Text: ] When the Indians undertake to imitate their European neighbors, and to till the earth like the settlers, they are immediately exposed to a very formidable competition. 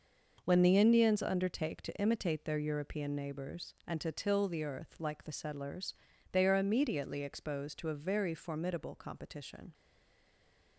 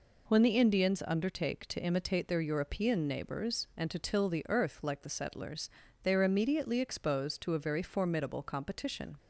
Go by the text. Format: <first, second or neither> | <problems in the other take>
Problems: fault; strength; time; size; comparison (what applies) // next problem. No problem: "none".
second | stays silent after the last word; from 9.7 s on; 1.0 s long